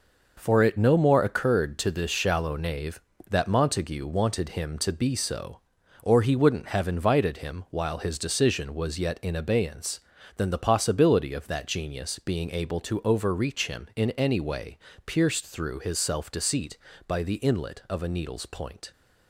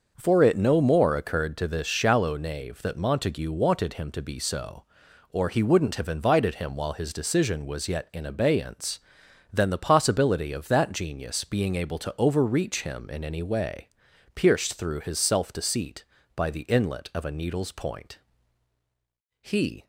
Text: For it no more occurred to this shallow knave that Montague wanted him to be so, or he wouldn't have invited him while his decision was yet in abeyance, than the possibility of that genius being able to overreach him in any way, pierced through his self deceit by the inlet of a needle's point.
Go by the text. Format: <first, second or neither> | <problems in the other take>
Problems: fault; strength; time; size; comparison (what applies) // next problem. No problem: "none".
first | starts louder than the rest; noticeable; until 1.1 s; 6 dB // goes on to say "He"; slight; from 19.4 s on; 0.44 s long